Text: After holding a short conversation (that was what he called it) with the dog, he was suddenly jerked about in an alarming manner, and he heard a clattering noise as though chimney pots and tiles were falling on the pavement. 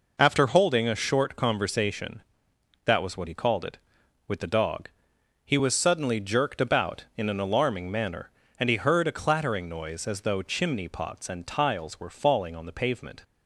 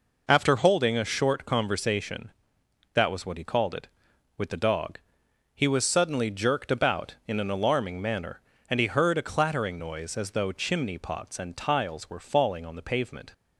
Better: neither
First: none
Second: none

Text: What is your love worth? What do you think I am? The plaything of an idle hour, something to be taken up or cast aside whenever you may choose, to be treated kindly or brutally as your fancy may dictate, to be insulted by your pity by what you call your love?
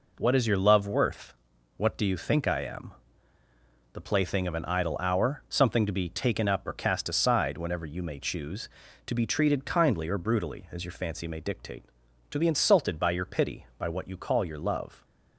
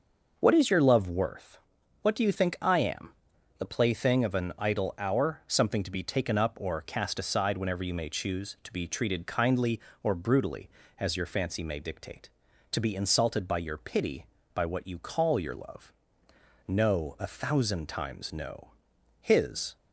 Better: first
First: none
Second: goes on to say "No a thousand times no His"; strong; from 16.6 s on; 3.0 s long

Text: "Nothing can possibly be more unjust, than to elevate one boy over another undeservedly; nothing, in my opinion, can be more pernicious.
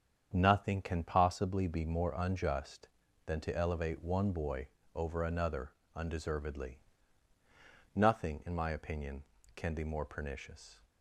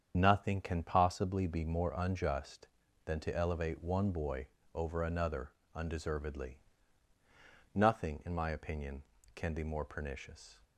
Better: first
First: starts louder than the rest; strong; until 1.3 s; 8 dB // pauses between "boy" and "over"; slight; at 4.6 s; 0.26 s long // pauses between "another" and "undeservedly"; slight; at 5.7 s; 0.22 s long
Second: loses the start of "Nothing"; at 0.1 s; 45 ms // starts louder than the rest; strong; until 1.1 s; 8 dB // pauses between "boy" and "over"; slight; at 4.4 s; 0.26 s long // pauses between "another" and "undeservedly"; slight; at 5.5 s; 0.22 s long

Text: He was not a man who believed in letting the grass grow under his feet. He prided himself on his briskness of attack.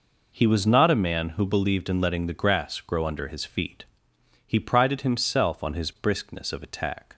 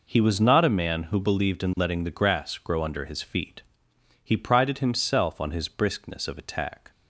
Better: neither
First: none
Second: none

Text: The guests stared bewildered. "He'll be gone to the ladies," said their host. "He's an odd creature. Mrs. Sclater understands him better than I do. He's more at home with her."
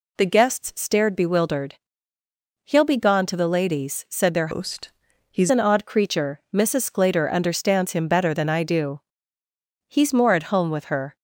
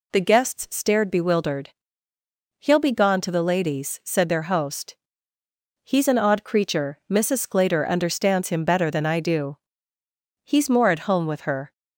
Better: second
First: changes voice from "host" to "He's"; from 4.5 to 5.5 s; 1.0 s long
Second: none

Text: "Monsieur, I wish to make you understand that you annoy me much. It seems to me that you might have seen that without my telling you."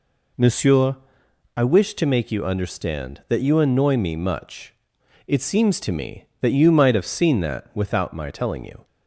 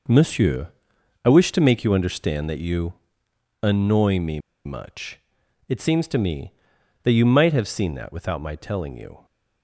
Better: first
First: none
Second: pauses between "you" and "annoy"; noticeable; at 2.9 s; 0.68 s long // pauses between "me" and "much"; slight; at 4.3 s; 0.26 s long

